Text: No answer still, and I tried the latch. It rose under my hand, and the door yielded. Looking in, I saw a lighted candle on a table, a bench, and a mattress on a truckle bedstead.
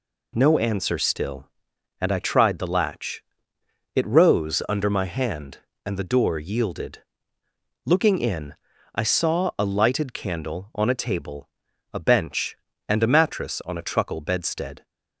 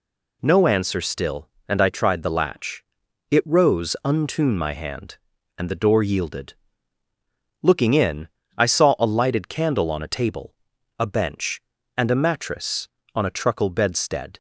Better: first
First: none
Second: says "untune" for "under"; at 4.0 s

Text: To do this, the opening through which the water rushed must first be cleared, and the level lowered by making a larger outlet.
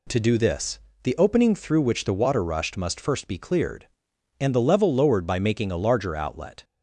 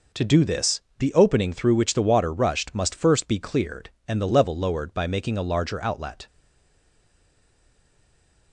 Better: first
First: none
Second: stays silent after the last word; from 6.2 s on; 2.3 s long

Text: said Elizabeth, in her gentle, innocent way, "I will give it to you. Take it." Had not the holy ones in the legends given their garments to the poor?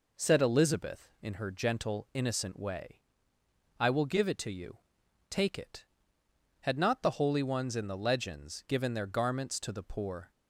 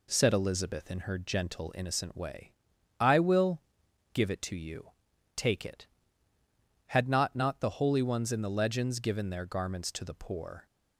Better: first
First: none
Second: pauses between "will" and "give"; noticeable; at 3.6 s; 0.52 s long // says "not" twice; at 7.3 s

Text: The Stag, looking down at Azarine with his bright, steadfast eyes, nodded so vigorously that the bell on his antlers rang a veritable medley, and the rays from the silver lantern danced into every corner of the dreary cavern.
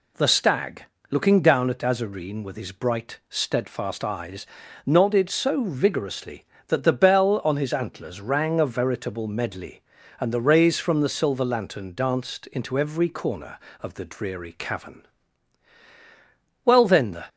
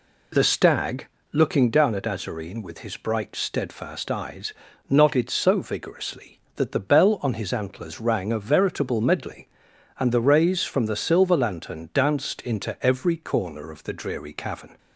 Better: second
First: goes on to say "Well then the"; from 16.6 s on; 0.60 s long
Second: none

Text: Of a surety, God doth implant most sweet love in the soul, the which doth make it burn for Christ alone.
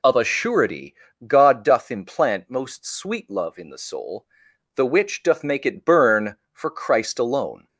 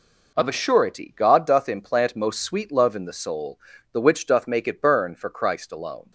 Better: neither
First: none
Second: none

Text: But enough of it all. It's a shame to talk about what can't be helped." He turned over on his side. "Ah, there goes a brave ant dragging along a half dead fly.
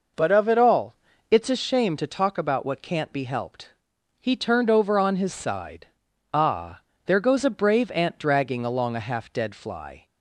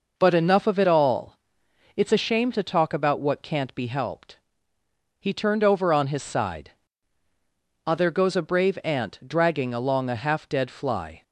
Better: second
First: skips "enough"; at 0.2 s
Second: none

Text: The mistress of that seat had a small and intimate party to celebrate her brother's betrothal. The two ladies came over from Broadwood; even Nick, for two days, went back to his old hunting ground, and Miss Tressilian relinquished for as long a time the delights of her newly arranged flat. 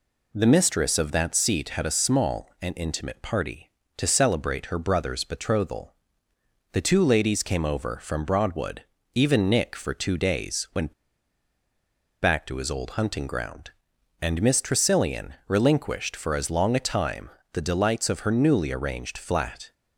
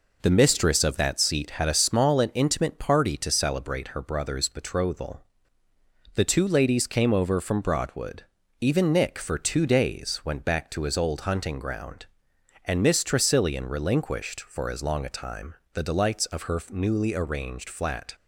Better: second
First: pauses between "went" and "back"; strong; at 10.9 s; 1.2 s long // pauses between "Tressilian" and "relinquished"; slight; at 15.3 s; 0.16 s long // pauses between "time" and "the"; slight; at 17.2 s; 0.22 s long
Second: pauses between "time" and "the"; slight; at 15.5 s; 0.18 s long

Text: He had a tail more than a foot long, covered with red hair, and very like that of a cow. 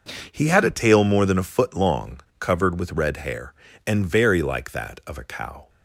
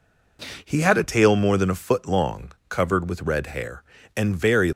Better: first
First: none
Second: stops before "like that of a cow"; at 4.7 s

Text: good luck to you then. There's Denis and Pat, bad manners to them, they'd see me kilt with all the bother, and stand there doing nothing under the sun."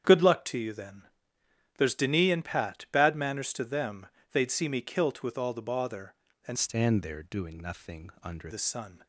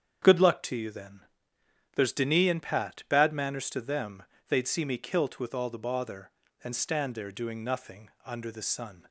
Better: second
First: starts louder than the rest; strong; until 1.8 s; 8.5 dB // changes voice from "stand" to "under"; from 6.5 to 8.5 s; 2.0 s long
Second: starts louder than the rest; strong; until 2.0 s; 8 dB

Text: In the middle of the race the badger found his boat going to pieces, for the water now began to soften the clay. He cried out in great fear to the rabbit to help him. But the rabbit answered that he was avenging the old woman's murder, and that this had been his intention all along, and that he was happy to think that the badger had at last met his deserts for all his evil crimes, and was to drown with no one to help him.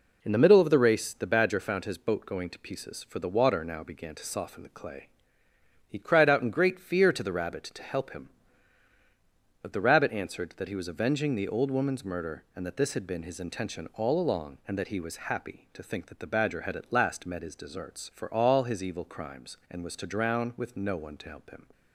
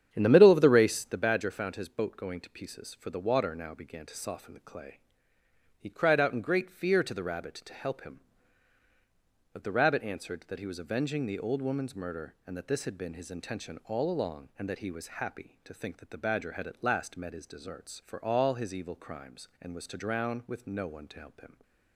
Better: first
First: none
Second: starts louder than the rest; strong; until 1.3 s; 9 dB

